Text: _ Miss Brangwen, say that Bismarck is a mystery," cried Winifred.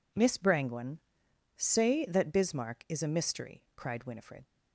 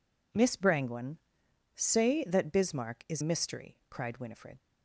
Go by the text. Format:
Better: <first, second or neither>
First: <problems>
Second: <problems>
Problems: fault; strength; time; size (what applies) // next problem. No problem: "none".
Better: first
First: none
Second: skips "a"; at 3.2 s